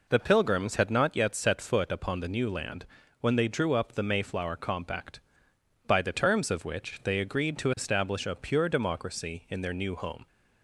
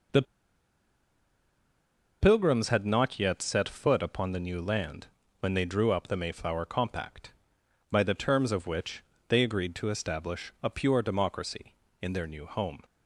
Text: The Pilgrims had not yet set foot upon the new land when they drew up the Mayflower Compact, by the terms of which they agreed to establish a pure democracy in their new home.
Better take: first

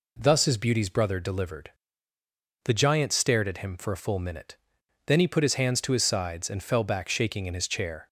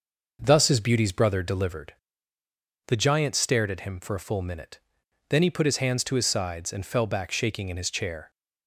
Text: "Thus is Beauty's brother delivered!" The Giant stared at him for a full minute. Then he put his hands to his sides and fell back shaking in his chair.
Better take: first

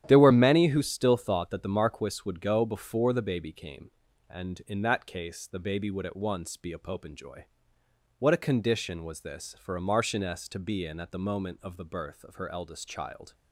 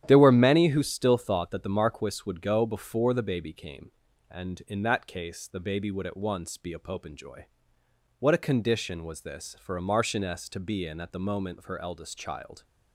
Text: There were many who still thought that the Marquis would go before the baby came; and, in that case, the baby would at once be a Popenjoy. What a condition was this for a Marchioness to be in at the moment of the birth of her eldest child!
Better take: first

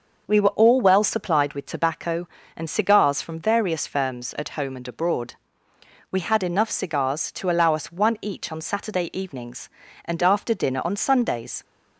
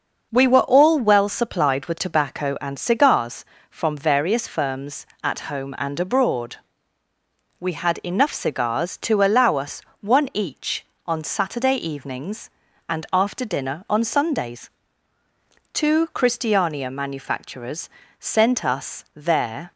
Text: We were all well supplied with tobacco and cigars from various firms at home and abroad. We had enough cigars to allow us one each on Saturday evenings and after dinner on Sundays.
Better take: first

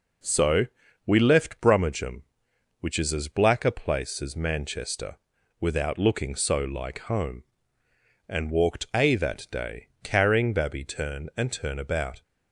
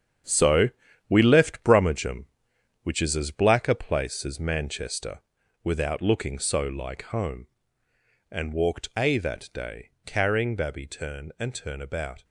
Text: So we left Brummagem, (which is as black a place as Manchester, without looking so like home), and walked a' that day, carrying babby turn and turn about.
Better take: first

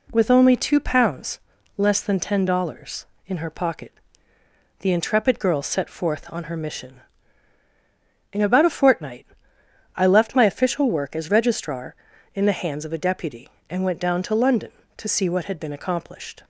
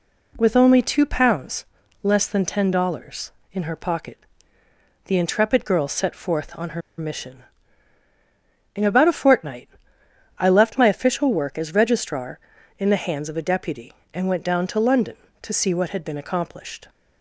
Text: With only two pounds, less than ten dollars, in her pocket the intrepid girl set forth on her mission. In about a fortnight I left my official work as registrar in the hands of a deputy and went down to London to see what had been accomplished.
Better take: first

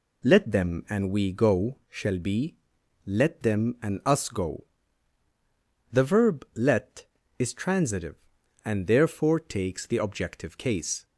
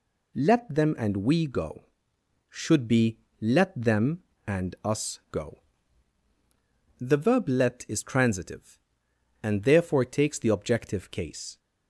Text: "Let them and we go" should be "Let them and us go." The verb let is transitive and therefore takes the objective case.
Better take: second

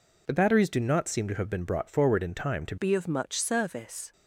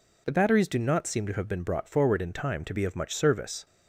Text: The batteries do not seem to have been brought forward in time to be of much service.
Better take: second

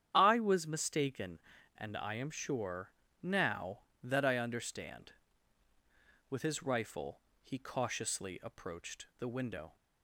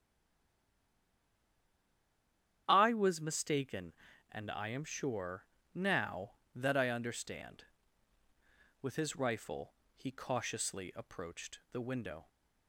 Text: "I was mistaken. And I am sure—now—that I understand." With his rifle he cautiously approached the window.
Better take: first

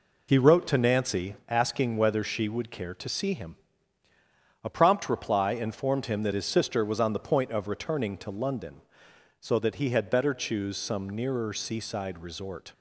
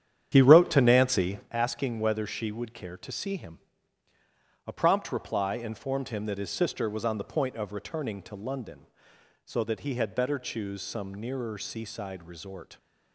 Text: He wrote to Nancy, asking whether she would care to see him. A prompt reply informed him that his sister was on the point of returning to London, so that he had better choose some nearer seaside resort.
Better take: first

